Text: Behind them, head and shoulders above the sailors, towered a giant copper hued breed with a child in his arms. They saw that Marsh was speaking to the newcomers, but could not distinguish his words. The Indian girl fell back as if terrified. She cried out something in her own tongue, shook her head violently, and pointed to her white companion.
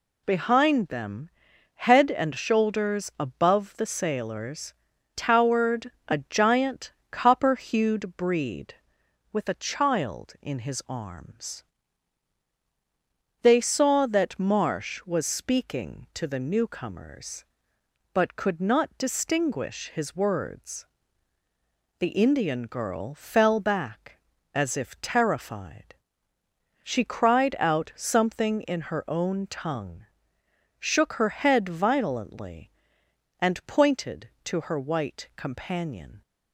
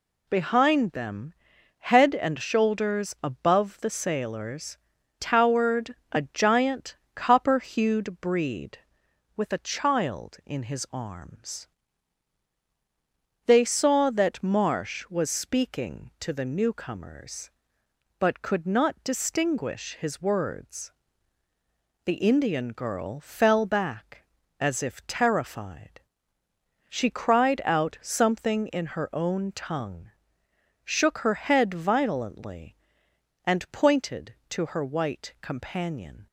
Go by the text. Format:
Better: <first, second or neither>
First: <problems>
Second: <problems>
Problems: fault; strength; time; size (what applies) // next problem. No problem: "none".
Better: neither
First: pauses between "towered" and "a"; slight; at 5.9 s; 0.16 s long // pauses between "giant" and "copper"; slight; at 6.9 s; 0.18 s long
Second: pauses between "towered" and "a"; slight; at 5.9 s; 0.16 s long // pauses between "giant" and "copper"; slight; at 6.9 s; 0.18 s long